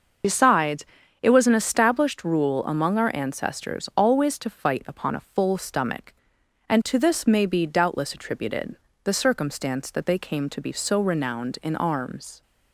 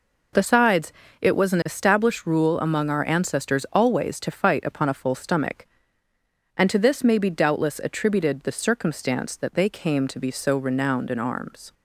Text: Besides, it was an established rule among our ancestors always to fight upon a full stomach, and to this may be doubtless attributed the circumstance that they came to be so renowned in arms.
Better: second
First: loses the start of "Besides"; at 0.2 s; 45 ms // starts louder than the rest; noticeable; until 1.6 s; 6 dB // pauses between "attributed" and "the"; slight; at 8.7 s; 0.30 s long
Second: none

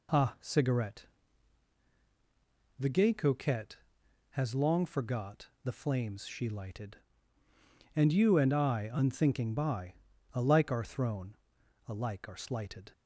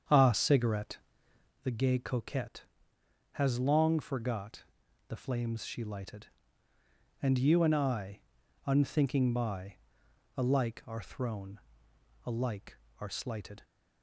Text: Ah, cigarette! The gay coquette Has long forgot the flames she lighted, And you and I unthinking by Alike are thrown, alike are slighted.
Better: first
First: pauses between "by" and "Alike"; at 9.9 s; 0.40 s long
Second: starts louder than the rest; strong; until 1.7 s; 7.5 dB // pauses between "forgot" and "the"; noticeable; at 4.6 s; 0.46 s long // pauses between "I" and "unthinking"; noticeable; at 8.1 s; 0.48 s long // pauses between "by" and "Alike"; noticeable; at 9.7 s; 0.60 s long

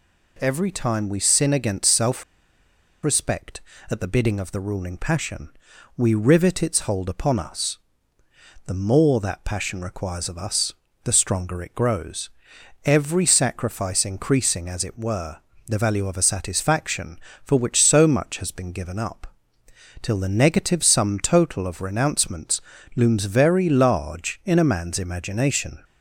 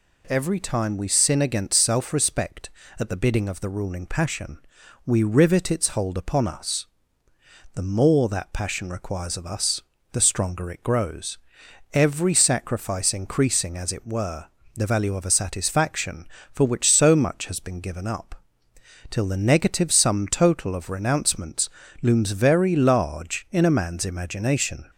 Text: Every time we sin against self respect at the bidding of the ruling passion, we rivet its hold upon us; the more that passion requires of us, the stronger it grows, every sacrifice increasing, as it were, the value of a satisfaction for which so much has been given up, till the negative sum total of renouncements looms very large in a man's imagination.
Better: second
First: pauses between "self" and "respect"; noticeable; at 2.2 s; 0.79 s long // pauses between "renouncements" and "looms"; slight; at 22.6 s; 0.34 s long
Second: pauses between "renouncements" and "looms"; slight; at 21.6 s; 0.32 s long

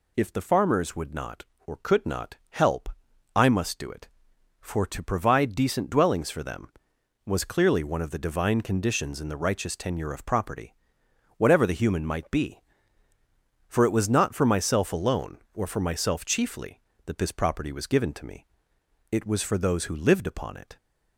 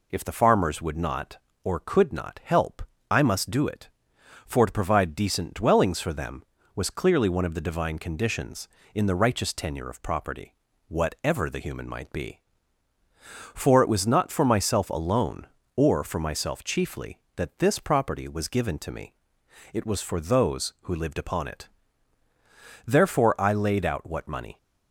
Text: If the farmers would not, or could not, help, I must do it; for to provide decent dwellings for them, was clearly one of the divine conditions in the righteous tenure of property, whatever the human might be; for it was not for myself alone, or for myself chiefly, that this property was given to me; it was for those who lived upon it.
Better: first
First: none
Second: goes on to say "Therefore I laid out what money"; strong; from 22.8 s on; 1.7 s long

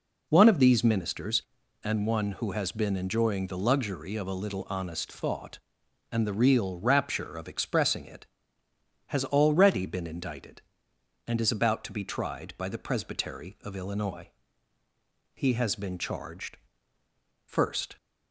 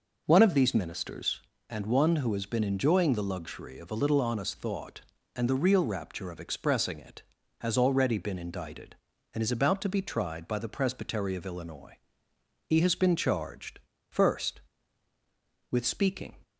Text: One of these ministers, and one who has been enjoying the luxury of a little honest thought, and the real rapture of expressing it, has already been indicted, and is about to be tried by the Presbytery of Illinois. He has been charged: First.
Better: first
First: none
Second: goes on to say "With speaking"; noticeable; from 15.7 s on; 0.64 s long

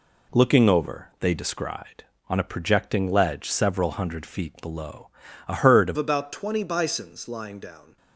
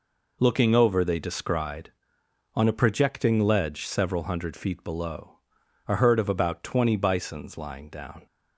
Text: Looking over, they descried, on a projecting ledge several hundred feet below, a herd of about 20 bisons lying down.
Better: second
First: changes voice at "about"; from 5.9 s on; 2.0 s long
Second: none

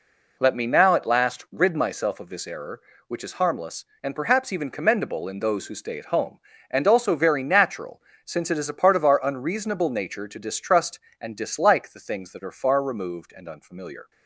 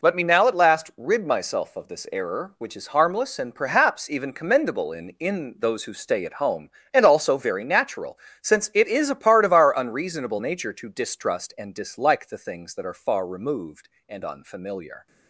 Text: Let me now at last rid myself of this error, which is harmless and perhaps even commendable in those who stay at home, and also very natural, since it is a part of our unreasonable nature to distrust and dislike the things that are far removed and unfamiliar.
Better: first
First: none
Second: says "in" twice; at 5.1 s

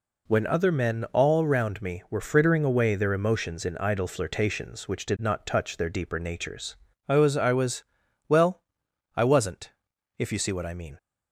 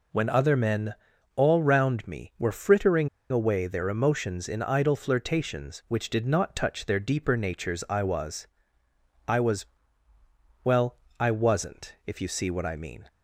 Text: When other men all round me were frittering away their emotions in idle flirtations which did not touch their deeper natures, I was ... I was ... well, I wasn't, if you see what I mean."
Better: first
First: none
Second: pauses between "men" and "all"; at 0.9 s; 0.42 s long // pauses between "frittering" and "away"; slight; at 3.0 s; 0.22 s long

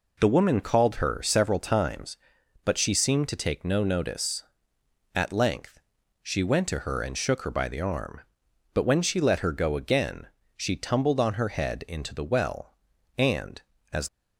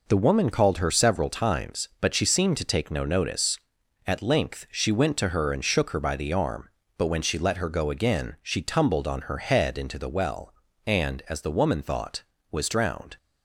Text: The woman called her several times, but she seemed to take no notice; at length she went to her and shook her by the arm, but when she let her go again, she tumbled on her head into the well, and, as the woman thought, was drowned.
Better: second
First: pauses between "length" and "she"; at 5.7 s; 0.44 s long // stops before "the woman thought was drowned"; at 14.0 s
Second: none

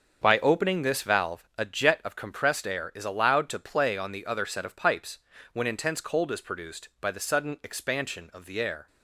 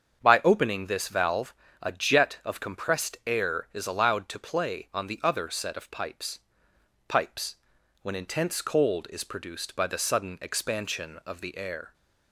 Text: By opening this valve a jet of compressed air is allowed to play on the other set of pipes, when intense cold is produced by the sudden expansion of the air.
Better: first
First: starts louder than the rest; until 1.2 s; 7 dB // pauses between "valve" and "a"; slight; at 1.4 s; 0.16 s long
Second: starts louder than the rest; strong; until 1.2 s; 7 dB // pauses between "valve" and "a"; slight; at 1.5 s; 0.28 s long // says "pipes" twice; at 7.0 s

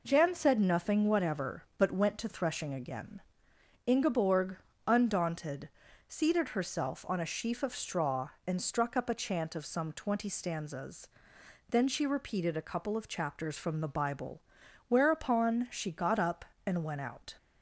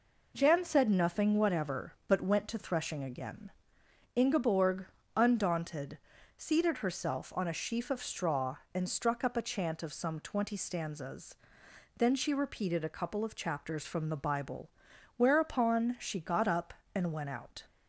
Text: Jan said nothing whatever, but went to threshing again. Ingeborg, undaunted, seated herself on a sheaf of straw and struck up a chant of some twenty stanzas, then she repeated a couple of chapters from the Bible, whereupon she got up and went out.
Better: neither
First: none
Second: none

